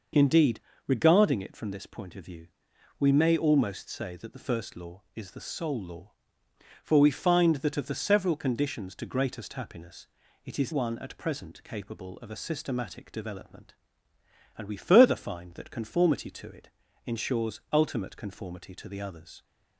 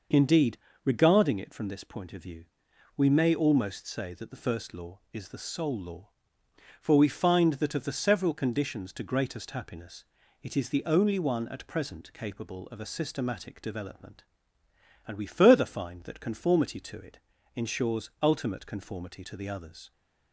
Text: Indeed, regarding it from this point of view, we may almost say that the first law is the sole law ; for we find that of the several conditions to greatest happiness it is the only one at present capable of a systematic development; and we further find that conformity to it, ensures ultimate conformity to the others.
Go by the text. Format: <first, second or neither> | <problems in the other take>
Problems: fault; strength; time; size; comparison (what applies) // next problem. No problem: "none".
second | pauses between "happiness" and "it"; at 10.0 s; 0.38 s long; also in the second // skips "the only"; at 10.7 s